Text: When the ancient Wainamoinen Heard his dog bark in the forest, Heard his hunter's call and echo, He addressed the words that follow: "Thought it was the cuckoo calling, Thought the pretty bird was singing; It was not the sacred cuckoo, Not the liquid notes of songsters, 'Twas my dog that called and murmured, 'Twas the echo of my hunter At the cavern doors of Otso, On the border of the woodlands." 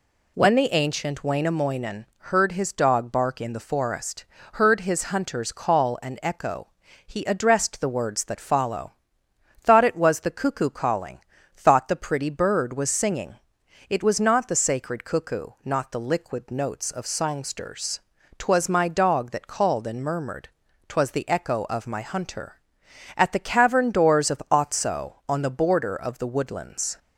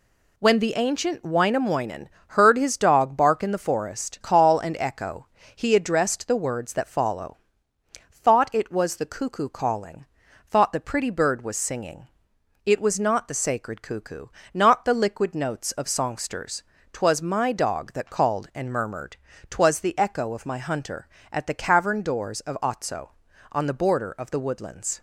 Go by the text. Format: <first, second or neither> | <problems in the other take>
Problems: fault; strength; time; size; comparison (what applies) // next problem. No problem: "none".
first | pauses between "Wainamoinen" and "Heard"; slight; at 2.0 s; 0.20 s long // skips "Heard his hunter's"; at 4.2 s